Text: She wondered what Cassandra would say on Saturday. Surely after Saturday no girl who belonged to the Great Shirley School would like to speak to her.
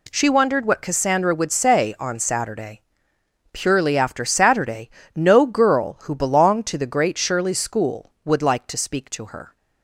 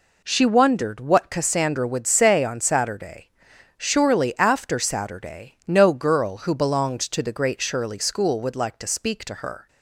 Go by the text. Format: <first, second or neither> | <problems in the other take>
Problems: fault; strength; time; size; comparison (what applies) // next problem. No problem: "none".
second | says "Purely" for "Surely"; at 3.5 s // pauses between "Saturday" and "no"; slight; at 4.8 s; 0.26 s long